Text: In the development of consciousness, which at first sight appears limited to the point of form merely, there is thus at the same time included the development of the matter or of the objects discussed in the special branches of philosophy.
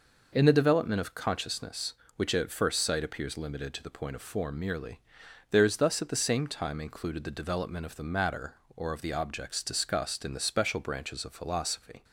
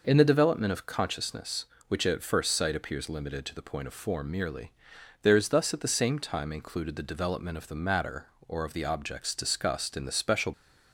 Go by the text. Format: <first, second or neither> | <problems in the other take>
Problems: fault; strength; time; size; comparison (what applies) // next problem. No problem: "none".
first | stops before "branches of philosophy"; at 10.5 s